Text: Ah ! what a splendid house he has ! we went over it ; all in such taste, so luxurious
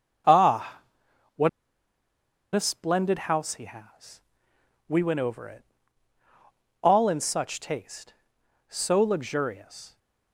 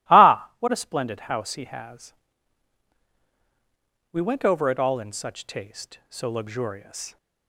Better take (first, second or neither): second